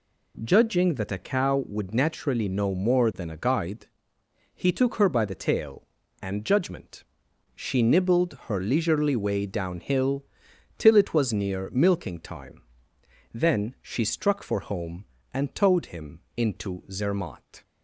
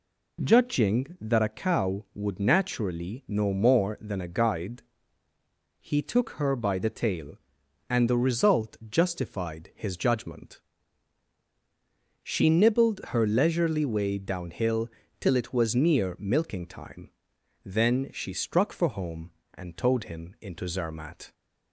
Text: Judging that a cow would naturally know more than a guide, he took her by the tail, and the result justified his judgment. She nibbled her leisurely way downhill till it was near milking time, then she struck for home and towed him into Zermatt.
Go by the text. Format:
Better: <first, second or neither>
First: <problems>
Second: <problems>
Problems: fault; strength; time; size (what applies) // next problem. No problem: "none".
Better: second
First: skips "the result justified his"; at 6.4 s // pauses between "downhill" and "till"; noticeable; at 10.2 s; 0.52 s long // pauses between "him" and "into"; slight; at 16.1 s; 0.16 s long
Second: pauses between "downhill" and "till"; slight; at 14.8 s; 0.32 s long